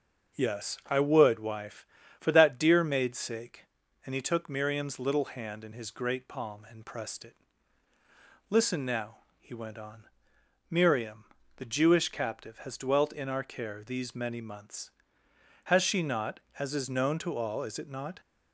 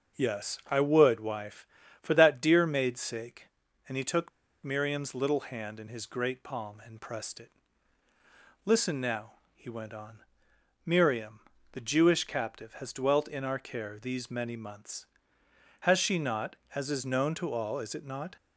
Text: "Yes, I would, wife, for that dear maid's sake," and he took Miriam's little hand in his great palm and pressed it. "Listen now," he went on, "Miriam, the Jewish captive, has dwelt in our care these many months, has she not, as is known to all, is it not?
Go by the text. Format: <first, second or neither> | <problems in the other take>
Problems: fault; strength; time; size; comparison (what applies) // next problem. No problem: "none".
first | starts louder than the rest; until 1.2 s; 6.5 dB; also in the first // pauses between "took" and "Miriam's"; slight; at 4.3 s; 0.33 s long